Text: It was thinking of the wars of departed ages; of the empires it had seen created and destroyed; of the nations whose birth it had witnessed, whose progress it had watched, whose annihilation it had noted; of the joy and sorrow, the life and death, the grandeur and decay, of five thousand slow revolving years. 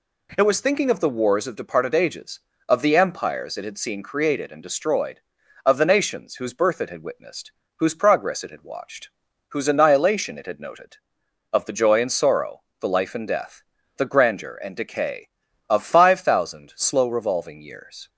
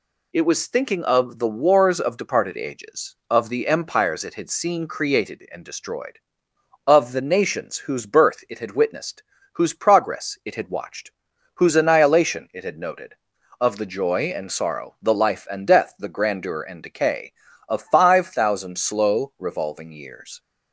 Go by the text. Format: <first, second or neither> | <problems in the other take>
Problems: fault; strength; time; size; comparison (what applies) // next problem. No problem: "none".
neither | none